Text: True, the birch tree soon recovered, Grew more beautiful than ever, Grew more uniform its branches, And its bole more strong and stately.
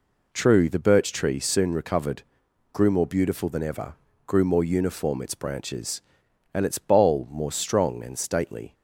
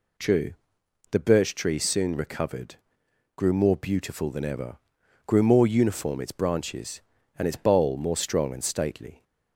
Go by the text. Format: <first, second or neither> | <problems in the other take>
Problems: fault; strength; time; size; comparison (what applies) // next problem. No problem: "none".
neither | none